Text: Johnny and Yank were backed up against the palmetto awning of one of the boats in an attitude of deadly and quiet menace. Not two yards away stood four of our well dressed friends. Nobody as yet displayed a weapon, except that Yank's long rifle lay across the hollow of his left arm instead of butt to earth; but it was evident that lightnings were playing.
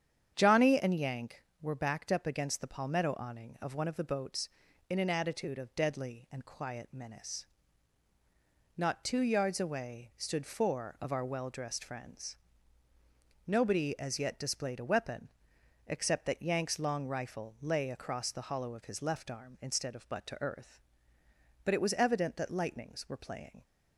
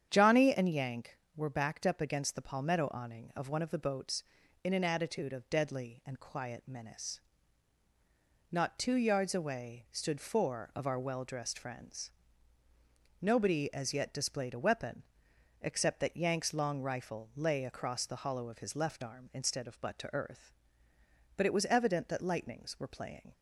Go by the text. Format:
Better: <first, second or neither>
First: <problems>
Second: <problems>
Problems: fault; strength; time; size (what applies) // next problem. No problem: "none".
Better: neither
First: starts louder than the rest; strong; until 1.3 s; 8.5 dB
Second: starts louder than the rest; strong; until 1.1 s; 8.5 dB